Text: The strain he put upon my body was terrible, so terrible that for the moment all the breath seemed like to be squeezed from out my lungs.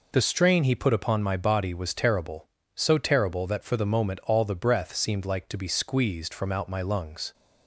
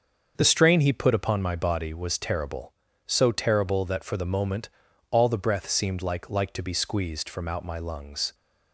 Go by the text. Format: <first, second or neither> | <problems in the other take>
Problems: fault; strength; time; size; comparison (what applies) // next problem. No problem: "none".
first | starts louder than the rest; until 1.3 s; 6.5 dB // pauses between "moment" and "all"; at 4.6 s; 0.42 s long // says "like" twice; at 6.2 s